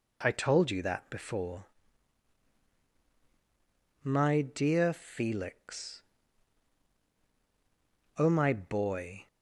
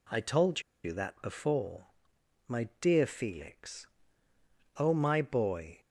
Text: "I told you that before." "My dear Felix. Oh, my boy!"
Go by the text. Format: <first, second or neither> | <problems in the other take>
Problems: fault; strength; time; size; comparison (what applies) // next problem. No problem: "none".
first | pauses between "told" and "you"; slight; at 0.6 s; 0.22 s long // pauses between "My" and "dear"; slight; at 2.6 s; 0.16 s long